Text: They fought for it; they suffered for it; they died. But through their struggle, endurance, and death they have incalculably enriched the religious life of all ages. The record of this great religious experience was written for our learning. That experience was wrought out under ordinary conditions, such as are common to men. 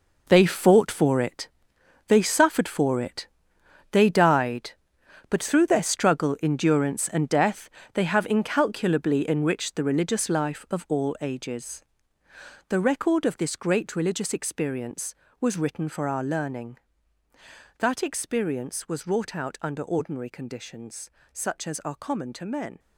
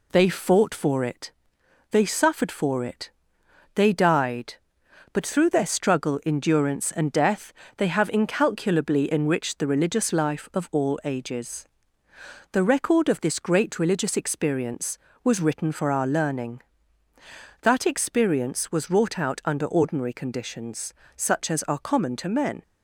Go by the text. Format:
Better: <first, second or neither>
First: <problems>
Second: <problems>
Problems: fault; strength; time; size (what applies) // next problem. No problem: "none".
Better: second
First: gets quieter; strong; throughout; 12 dB // pauses between "death" and "they"; slight; at 7.6 s; 0.24 s long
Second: pauses between "death" and "they"; slight; at 7.5 s; 0.24 s long